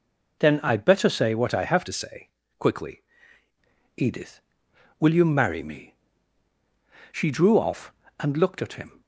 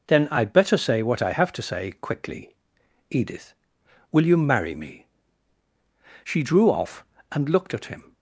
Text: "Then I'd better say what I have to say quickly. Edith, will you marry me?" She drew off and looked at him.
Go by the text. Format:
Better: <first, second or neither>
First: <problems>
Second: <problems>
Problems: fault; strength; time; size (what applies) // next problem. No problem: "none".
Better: second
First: changes voice from "to" to "quickly"; from 1.8 to 3.0 s; 1.2 s long // pauses between "say" and "quickly"; slight; at 2.2 s; 0.32 s long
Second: none